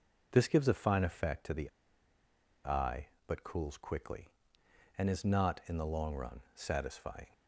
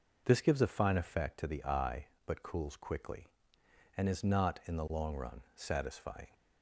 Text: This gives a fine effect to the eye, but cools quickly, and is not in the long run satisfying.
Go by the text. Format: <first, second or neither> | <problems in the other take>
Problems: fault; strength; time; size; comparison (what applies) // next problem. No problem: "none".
second | pauses between "the" and "eye"; noticeable; at 1.6 s; 0.96 s long // pauses between "run" and "satisfying"; slight; at 6.4 s; 0.16 s long; slight in the second